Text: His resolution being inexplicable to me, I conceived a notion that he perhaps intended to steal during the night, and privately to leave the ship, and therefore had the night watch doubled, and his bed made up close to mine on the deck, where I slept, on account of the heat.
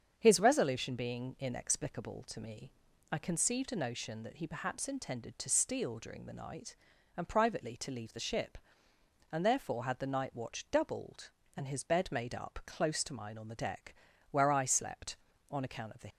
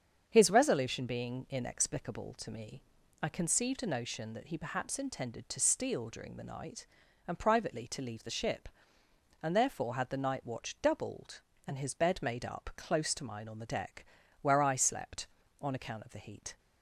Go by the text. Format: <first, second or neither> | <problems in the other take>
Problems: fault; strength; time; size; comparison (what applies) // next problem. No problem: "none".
second | starts louder than the rest; strong; until 1.1 s; 7.5 dB; strong in the second // stops before "heat"; at 16.0 s